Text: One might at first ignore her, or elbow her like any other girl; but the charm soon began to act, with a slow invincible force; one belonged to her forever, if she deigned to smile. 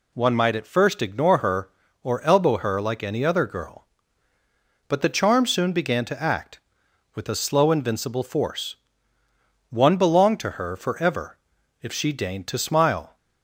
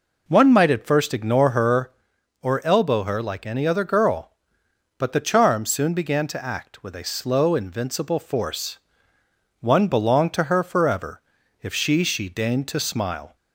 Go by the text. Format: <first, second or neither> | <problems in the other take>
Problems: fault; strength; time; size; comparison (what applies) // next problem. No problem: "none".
first | says "she" twice; at 12.0 s